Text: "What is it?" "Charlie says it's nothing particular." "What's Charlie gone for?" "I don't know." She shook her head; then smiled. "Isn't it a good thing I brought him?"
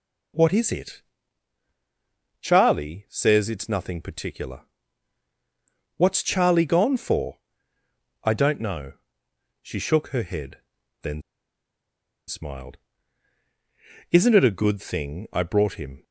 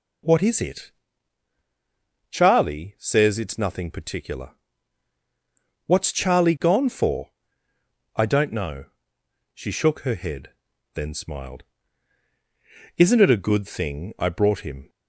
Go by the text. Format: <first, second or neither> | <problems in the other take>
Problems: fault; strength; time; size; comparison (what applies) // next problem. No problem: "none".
second | pauses between "then" and "smiled"; at 11.2 s; 1.0 s long